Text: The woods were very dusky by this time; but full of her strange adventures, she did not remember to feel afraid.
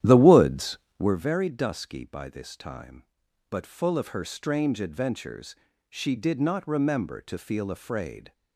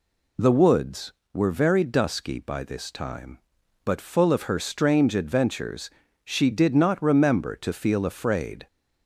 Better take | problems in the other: second | starts louder than the rest; strong; until 1.3 s; 11 dB

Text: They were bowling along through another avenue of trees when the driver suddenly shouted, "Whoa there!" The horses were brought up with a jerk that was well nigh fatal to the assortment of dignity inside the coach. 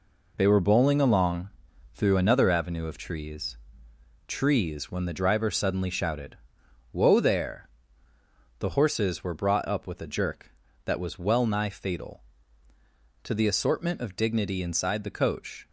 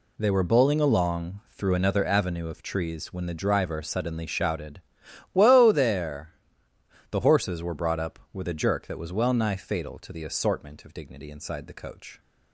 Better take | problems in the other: second | pauses between "along" and "through"; at 1.4 s; 0.44 s long // says "trees" twice; at 4.2 s

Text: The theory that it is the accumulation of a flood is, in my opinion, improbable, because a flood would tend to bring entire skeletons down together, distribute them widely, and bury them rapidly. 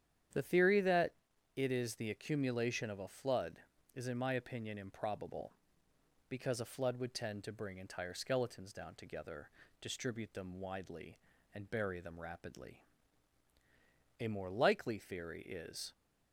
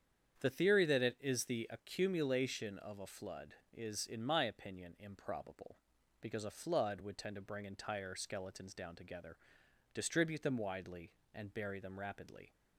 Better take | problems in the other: second | starts louder than the rest; strong; until 1.8 s; 9.5 dB; strong in the second // pauses between "that" and "it"; noticeable; at 1.1 s; 0.46 s long // goes on to say "A more likely theory is"; strong; from 14.2 s on; 1.7 s long

